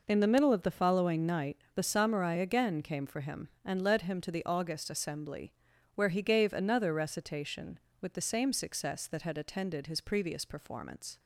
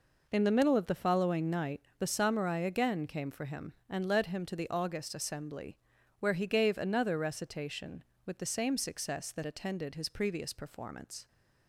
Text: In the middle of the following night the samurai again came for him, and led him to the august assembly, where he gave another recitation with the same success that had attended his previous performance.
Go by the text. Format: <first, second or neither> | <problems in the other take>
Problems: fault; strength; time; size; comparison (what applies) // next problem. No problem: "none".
first | pauses between "night" and "the"; slight; at 1.7 s; 0.20 s long; slight in the first // skips "had"; at 9.4 s